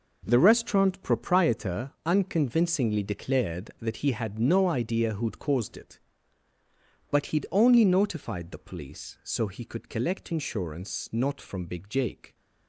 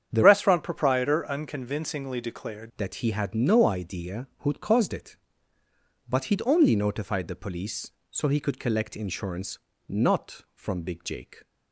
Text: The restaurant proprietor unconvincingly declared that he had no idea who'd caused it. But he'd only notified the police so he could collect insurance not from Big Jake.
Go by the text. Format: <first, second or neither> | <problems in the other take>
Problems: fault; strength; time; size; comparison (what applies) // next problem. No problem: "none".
first | starts louder than the rest; strong; until 1.1 s; 8.5 dB // changes voice from "restaurant" to "declared"; from 0.2 to 2.6 s; 2.4 s long // pauses between "insurance" and "not"; slight; at 9.5 s; 0.30 s long